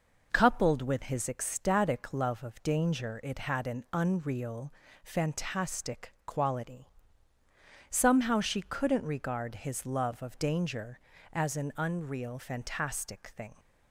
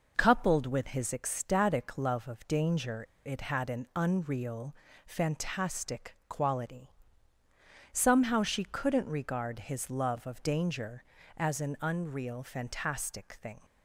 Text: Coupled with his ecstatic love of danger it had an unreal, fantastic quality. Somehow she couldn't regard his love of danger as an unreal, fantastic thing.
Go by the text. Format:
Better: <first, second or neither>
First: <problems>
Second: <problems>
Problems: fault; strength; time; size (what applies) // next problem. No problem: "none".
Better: first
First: none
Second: pauses between "danger" and "it"; slight; at 3.0 s; 0.21 s long